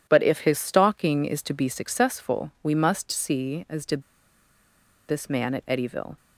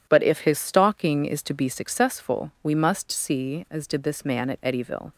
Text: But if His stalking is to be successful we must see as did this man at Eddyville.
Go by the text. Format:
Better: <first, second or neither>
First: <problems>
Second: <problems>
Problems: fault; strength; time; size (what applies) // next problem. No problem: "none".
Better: second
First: pauses between "did" and "this"; at 4.0 s; 1.0 s long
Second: none